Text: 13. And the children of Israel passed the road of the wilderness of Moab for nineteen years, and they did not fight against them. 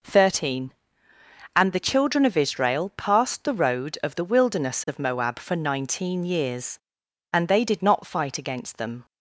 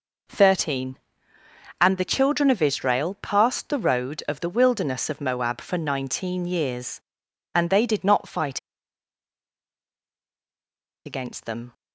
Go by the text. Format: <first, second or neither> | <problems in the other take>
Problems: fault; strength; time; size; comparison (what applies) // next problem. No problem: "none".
first | pauses between "fight" and "against"; strong; at 8.5 s; 2.4 s long